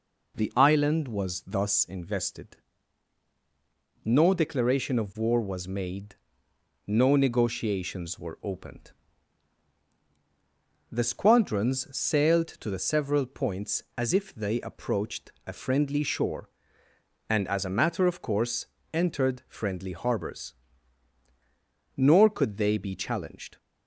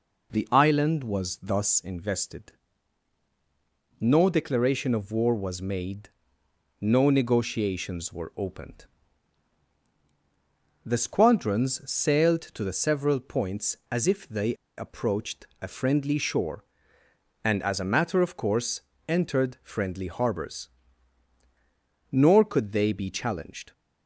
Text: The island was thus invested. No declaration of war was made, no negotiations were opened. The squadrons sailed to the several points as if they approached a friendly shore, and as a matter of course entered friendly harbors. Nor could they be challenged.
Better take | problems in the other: first | pauses between "they" and "approached"; slight; at 14.5 s; 0.22 s long // pauses between "approached" and "a"; slight; at 15.4 s; 0.16 s long; slight in the first // pauses between "course" and "entered"; slight; at 18.8 s; 0.26 s long; slight in the first

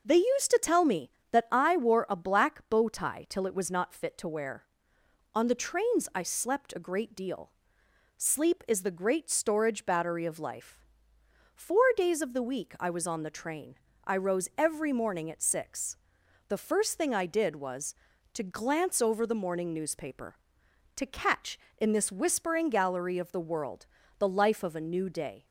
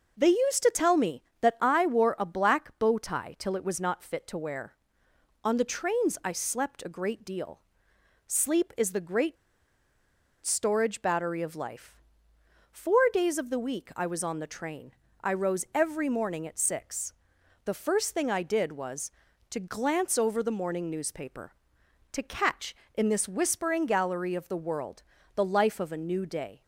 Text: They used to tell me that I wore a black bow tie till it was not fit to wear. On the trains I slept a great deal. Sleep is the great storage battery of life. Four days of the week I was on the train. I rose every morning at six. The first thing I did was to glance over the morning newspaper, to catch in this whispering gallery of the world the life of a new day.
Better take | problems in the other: first | pauses between "great" and "storage"; at 9.3 s; 1.0 s long // pauses between "world" and "the"; slight; at 25.0 s; 0.32 s long; slight in the first

